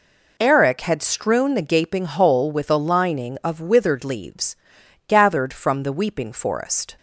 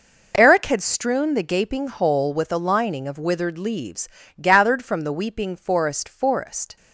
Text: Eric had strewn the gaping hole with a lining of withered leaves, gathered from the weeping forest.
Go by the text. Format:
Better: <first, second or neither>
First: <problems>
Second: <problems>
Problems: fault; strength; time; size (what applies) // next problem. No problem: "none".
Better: first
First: none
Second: says "forest" twice; at 6.0 s